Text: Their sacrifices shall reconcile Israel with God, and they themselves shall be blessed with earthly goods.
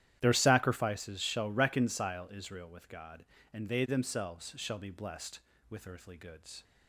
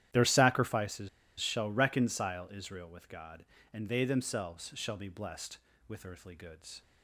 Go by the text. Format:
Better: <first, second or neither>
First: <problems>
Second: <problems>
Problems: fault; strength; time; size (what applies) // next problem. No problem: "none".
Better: first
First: starts louder than the rest; strong; until 1.2 s; 11.5 dB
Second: starts louder than the rest; strong; until 1.4 s; 11.5 dB // pauses between "sacrifices" and "shall"; slight; at 1.0 s; 0.30 s long